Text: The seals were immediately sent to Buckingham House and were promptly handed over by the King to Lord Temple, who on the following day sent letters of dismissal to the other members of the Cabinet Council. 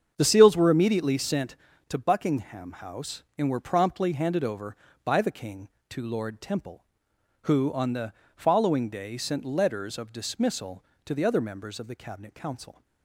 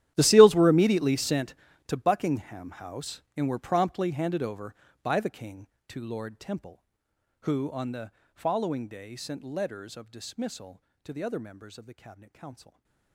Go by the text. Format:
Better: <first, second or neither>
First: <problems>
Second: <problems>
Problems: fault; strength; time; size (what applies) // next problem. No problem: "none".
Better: first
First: starts louder than the rest; strong; until 1.1 s; 7.5 dB // pauses between "the" and "following"; slight; at 8.1 s; 0.24 s long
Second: gets quieter; strong; throughout; 21 dB // starts louder than the rest; strong; until 1.1 s; 12 dB // pauses between "the" and "following"; slight; at 8.1 s; 0.24 s long // stays silent after the last word; slight; from 12.5 s on; 0.6 s long